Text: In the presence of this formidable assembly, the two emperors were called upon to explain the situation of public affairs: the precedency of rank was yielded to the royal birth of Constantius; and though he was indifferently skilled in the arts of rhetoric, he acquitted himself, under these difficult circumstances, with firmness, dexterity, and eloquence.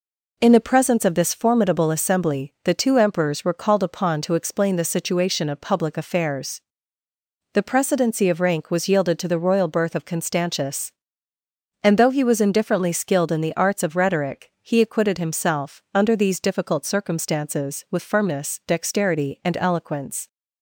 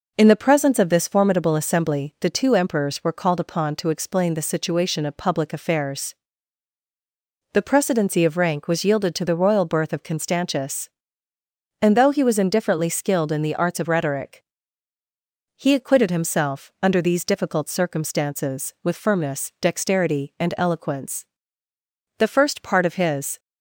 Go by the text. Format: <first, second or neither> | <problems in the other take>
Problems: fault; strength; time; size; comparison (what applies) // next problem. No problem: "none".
first | goes on to say "The first part of his"; noticeable; from 22.1 s on; 1.2 s long